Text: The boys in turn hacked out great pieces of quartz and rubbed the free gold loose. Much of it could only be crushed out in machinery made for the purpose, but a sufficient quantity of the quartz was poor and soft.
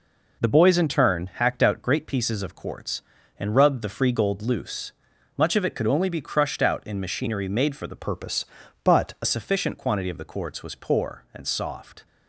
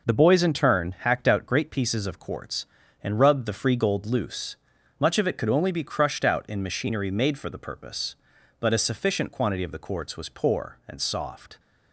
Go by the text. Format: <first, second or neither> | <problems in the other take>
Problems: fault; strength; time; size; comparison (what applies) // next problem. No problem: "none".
second | changes voice from "purpose" to "a"; from 7.9 to 9.2 s; 1.3 s long